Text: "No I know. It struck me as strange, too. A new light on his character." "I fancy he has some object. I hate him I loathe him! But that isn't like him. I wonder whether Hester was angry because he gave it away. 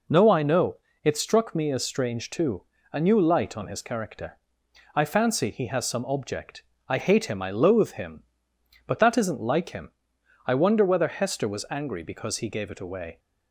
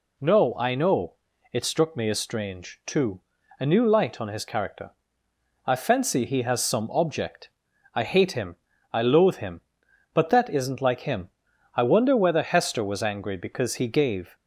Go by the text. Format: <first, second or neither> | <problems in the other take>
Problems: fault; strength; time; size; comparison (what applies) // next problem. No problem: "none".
first | pauses between "him" and "I"; slight; at 8.5 s; 0.36 s long // stops before "it away"; at 14.3 s